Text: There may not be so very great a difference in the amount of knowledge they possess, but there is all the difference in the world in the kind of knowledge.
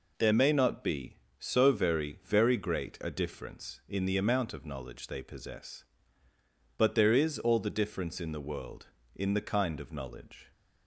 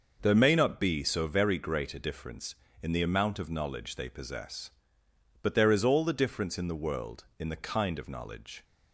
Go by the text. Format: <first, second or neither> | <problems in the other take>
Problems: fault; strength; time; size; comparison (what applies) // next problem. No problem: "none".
second | says "very" twice; at 2.2 s